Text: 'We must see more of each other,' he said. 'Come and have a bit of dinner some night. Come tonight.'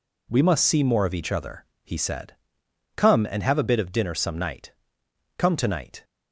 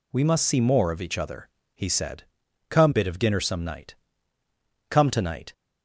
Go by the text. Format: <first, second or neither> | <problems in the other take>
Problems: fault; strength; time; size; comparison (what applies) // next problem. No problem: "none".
first | skips "and have a"; at 2.9 s